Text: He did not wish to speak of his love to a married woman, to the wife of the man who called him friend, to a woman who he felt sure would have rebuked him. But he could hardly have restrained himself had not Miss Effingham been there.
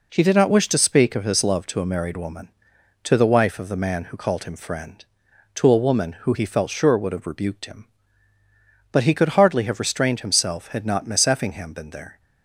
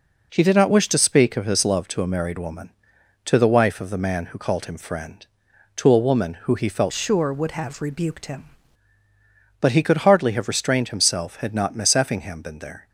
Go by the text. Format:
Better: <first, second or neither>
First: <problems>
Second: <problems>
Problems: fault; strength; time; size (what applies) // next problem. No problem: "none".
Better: first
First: none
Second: changes voice from "sure" to "him"; from 6.9 to 8.4 s; 1.5 s long